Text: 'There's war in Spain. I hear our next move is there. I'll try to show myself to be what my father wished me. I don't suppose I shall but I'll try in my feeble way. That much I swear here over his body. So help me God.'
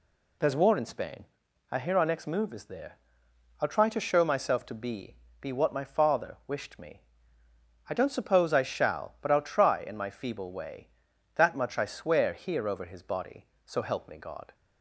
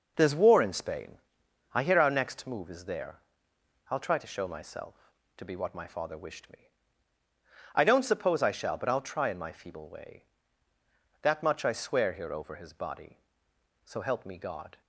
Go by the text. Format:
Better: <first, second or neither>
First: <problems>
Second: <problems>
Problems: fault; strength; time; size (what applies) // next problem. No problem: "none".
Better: second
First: says "be" twice; at 5.4 s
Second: none